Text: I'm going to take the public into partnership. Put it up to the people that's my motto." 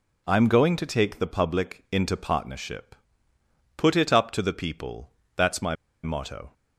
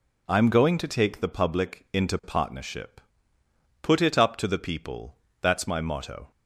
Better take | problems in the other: second | pauses between "people" and "that's"; slight; at 5.0 s; 0.26 s long; slight in the second // pauses between "my" and "motto"; slight; at 5.7 s; 0.30 s long

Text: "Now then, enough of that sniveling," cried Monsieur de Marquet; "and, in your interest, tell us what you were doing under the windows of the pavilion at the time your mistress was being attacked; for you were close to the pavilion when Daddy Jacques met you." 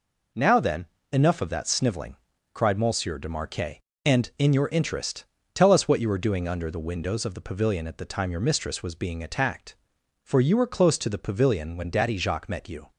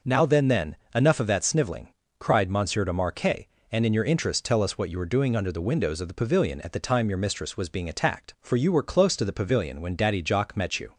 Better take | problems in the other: first | says "then" twice; at 0.4 s

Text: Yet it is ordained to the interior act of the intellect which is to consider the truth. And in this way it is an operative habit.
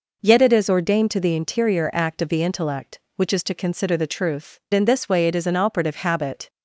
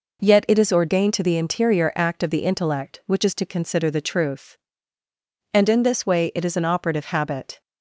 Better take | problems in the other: second | skips "And"; at 4.6 s

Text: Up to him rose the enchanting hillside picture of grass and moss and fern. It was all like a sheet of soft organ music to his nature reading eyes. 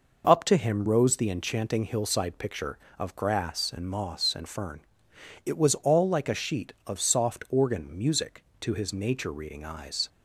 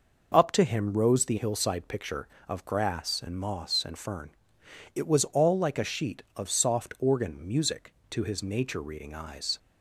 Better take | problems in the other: first | skips "enchanting"; at 1.3 s

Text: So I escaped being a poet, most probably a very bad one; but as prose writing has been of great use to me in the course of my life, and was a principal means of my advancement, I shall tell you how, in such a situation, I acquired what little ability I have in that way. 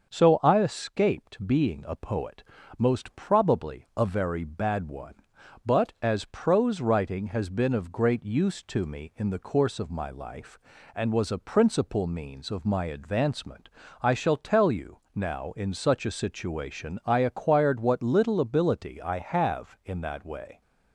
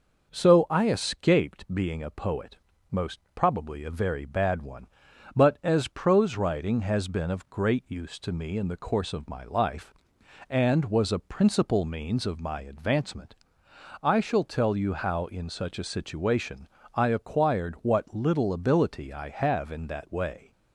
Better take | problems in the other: second | starts louder than the rest; until 1.1 s; 6.5 dB // says "now" for "how"; at 15.1 s

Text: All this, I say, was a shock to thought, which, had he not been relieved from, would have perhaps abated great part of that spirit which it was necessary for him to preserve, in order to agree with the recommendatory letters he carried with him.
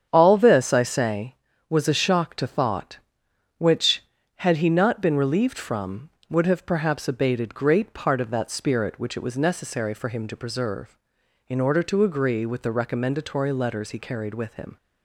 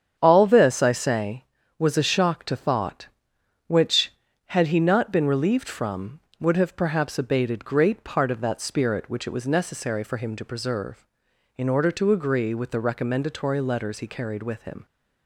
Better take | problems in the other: neither | starts louder than the rest; strong; the same in both

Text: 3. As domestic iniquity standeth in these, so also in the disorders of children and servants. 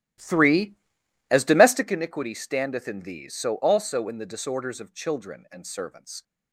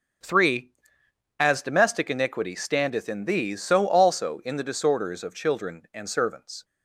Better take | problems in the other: second | starts louder than the rest; strong; until 2.0 s; 14.5 dB

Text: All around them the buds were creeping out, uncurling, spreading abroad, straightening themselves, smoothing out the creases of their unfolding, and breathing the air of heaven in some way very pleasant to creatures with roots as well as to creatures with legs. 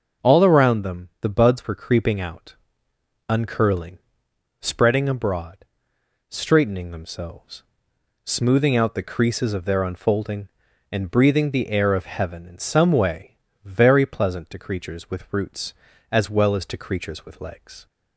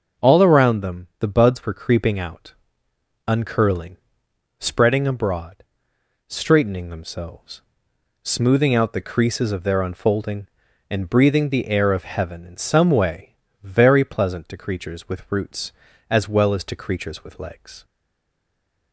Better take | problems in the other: first | starts louder than the rest; noticeable; until 1.3 s; 6 dB; noticeable in the first // pauses between "way" and "very"; slight; at 13.3 s; 0.26 s long; slight in the first // stays silent after the last word; from 17.8 s on; 1.1 s long

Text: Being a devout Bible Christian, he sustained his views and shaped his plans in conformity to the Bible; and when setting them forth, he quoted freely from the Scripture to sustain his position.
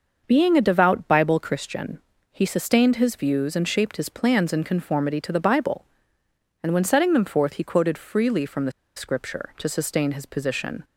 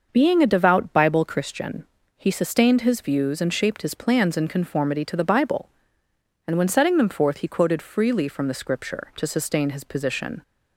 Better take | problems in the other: second | starts louder than the rest; noticeable; until 1.2 s; 6 dB; noticeable in the second // pauses between "the" and "Scripture"; slight; at 8.7 s; 0.24 s long

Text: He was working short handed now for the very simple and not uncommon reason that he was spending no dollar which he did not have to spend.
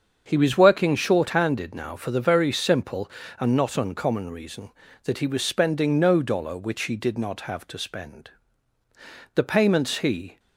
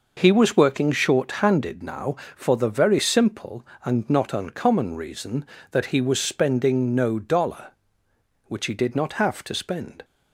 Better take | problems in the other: second | starts louder than the rest; until 1.2 s; 7 dB // goes on to say "The payments he"; noticeable; from 9.3 s on; 1.0 s long

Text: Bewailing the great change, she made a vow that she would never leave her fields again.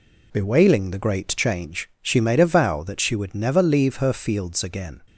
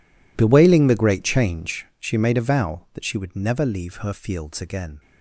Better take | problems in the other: first | gets quieter; strong; throughout; 19 dB

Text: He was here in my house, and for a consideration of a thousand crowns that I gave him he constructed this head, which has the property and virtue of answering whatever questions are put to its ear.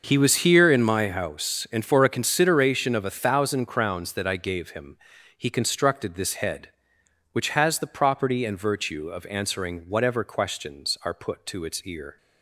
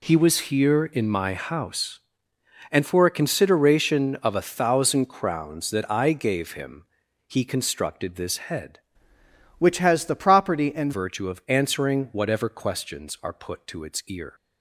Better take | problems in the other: first | pauses between "him" and "he"; at 6.8 s; 0.42 s long; also in the first // changes voice from "which" to "and"; from 9.5 to 10.9 s; 1.4 s long

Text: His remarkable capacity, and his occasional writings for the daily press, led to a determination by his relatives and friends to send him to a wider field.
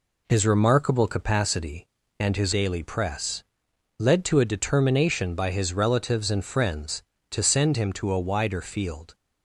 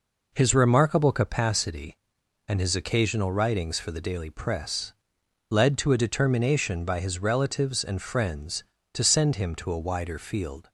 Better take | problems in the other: second | skips "occasional writings for the"; at 2.5 s

